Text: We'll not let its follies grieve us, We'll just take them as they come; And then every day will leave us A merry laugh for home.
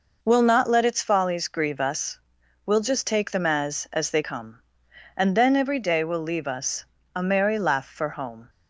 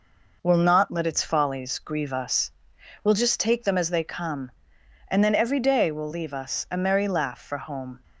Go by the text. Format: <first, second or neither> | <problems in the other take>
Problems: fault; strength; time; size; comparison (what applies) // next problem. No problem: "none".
second | says "as" twice; at 3.9 s // pauses between "us" and "A"; slight; at 6.8 s; 0.32 s long